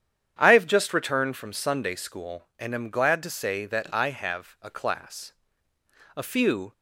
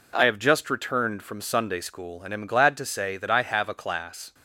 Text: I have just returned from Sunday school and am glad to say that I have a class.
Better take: second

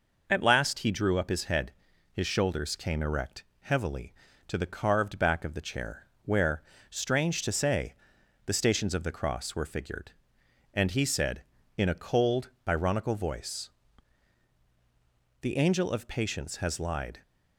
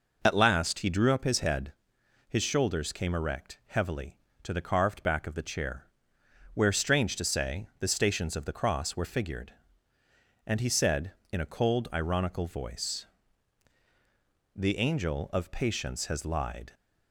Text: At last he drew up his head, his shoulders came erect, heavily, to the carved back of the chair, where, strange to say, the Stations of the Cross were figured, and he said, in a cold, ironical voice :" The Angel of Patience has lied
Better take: neither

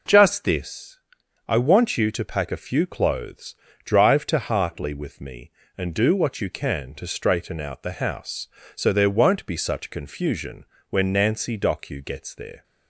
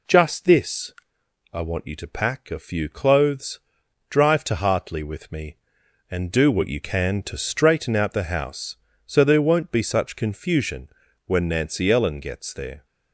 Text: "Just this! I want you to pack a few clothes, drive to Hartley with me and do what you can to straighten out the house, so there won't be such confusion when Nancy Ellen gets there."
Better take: second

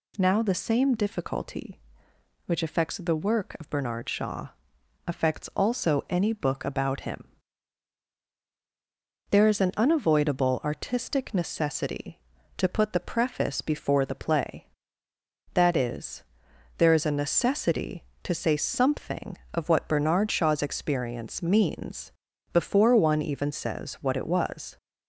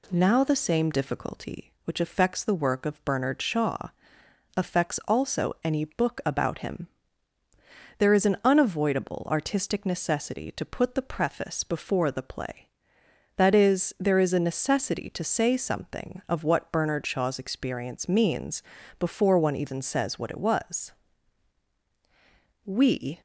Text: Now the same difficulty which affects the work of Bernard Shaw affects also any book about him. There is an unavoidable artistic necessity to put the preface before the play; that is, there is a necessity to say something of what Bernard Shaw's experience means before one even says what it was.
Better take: first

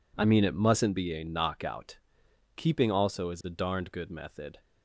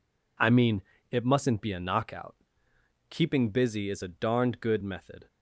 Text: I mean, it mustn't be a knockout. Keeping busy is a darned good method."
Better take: second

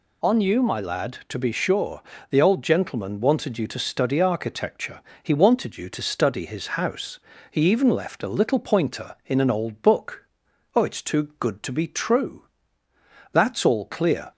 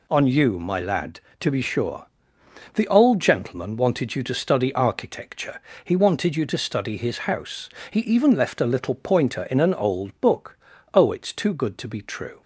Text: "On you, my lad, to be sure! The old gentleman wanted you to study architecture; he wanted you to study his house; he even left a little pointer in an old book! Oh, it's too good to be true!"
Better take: second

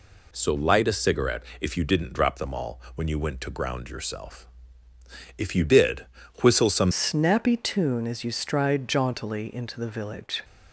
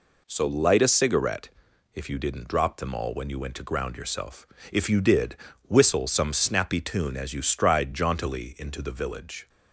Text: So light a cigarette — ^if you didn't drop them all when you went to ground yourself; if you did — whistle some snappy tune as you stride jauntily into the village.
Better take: second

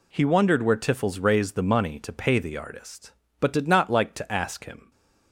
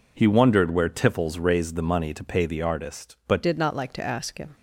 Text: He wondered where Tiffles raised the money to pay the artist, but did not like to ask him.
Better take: first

